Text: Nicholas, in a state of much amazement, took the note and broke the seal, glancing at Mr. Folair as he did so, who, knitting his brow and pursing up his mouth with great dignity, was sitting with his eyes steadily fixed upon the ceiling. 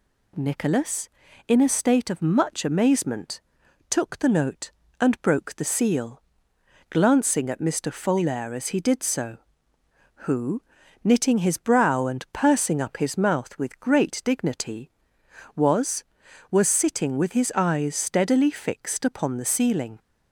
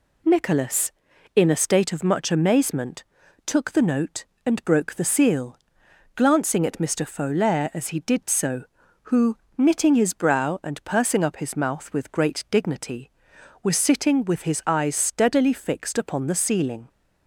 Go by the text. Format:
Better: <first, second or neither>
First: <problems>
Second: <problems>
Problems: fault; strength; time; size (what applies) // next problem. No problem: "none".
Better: second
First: says "was" twice; at 16.5 s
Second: none